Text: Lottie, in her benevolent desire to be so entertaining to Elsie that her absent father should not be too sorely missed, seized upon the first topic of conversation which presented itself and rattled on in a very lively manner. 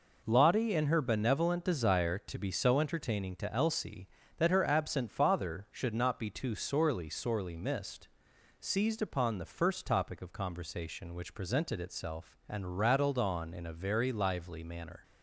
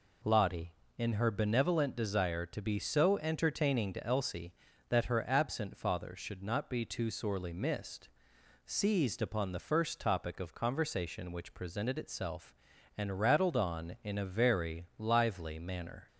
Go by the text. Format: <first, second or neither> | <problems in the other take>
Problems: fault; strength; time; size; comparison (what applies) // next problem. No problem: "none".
second | says "sorely" twice; at 7.0 s